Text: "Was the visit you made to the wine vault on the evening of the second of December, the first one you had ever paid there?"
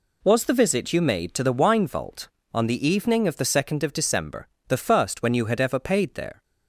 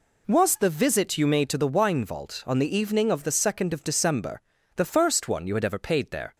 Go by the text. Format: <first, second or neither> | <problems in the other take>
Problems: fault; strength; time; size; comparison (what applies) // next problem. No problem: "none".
second | says "when" for "one"; at 5.2 s